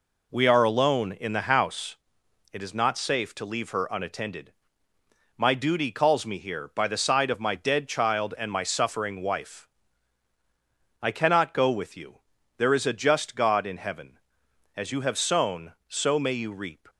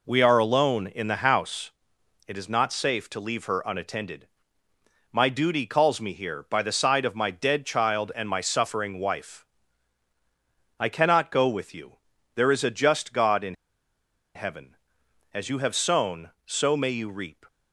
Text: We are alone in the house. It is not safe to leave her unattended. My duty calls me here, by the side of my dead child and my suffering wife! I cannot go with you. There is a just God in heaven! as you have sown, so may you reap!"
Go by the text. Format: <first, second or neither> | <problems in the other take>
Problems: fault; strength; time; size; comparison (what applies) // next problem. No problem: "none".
first | pauses between "in" and "heaven"; noticeable; at 13.5 s; 0.80 s long